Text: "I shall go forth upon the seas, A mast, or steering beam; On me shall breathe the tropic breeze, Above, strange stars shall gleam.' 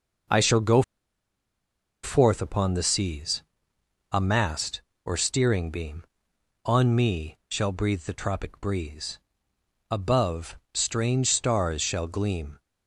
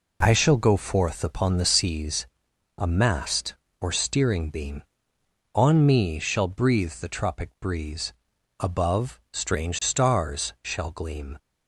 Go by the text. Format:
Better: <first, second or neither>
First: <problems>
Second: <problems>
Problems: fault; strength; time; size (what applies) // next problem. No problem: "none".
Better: second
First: pauses between "go" and "forth"; at 0.8 s; 1.2 s long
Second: none